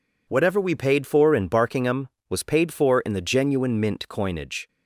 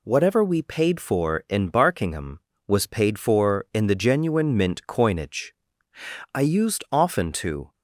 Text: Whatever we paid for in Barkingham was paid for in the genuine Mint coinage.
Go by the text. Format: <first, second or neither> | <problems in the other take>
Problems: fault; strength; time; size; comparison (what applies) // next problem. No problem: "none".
first | goes on to say "I used often to"; from 6.3 s on; 1.4 s long